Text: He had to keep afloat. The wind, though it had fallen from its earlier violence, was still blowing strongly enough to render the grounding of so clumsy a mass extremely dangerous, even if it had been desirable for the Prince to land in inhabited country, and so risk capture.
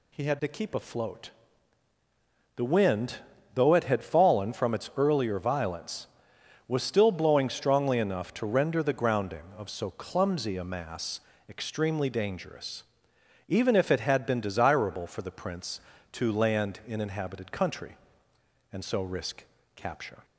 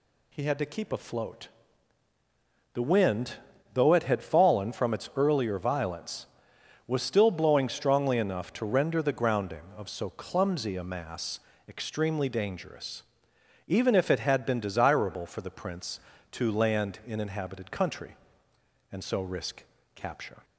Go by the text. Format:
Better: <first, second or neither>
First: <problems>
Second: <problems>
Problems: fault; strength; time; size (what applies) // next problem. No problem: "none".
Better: neither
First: pauses between "mass" and "extremely"; slight; at 11.1 s; 0.30 s long // pauses between "risk" and "capture"; slight; at 19.4 s; 0.32 s long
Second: pauses between "mass" and "extremely"; slight; at 11.3 s; 0.30 s long // pauses between "risk" and "capture"; slight; at 19.6 s; 0.32 s long